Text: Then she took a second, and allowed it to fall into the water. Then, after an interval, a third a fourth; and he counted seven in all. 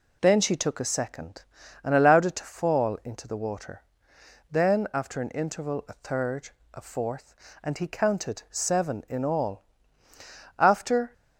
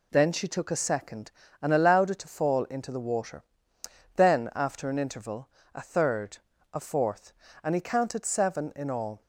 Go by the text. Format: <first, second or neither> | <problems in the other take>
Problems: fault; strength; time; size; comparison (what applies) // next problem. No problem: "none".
second | pauses between "third" and "a"; slight; at 6.4 s; 0.24 s long; slight in the second // goes on to say "After"; from 10.5 s on; 0.54 s long